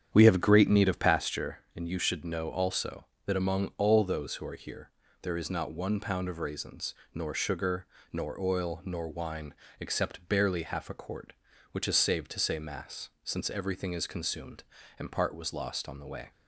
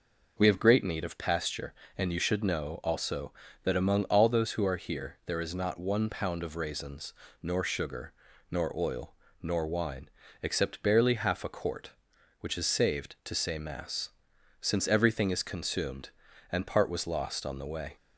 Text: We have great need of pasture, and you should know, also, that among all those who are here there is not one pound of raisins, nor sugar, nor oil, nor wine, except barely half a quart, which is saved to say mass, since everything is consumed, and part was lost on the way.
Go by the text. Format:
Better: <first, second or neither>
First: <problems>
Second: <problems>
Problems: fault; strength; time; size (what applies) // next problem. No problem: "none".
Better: second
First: starts louder than the rest; strong; until 1.5 s; 9 dB // pauses between "here" and "there"; slight; at 4.8 s; 0.32 s long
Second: none